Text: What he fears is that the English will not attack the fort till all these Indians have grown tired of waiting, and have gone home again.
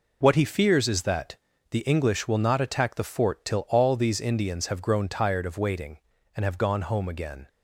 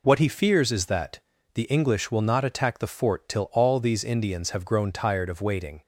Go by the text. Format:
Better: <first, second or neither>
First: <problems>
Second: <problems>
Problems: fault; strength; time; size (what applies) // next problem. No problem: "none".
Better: first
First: pauses between "that" and "the"; at 1.3 s; 0.38 s long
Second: pauses between "that" and "the"; at 1.1 s; 0.38 s long // stops before "and have gone home again"; at 5.8 s